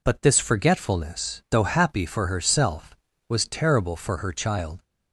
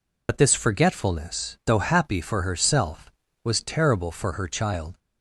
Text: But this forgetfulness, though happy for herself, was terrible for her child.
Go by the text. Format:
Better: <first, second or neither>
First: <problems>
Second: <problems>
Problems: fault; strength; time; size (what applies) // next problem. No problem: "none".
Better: first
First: none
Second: loses the start of "But"; at 0.2 s; 50 ms